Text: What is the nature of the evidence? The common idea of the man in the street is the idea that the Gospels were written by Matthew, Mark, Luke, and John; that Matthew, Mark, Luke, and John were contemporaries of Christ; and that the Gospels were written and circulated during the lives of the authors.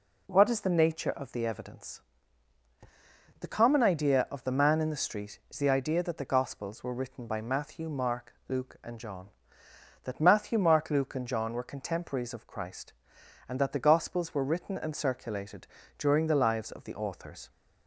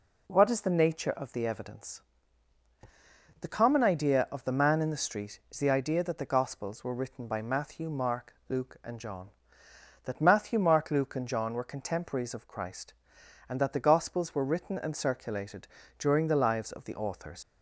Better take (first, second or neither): first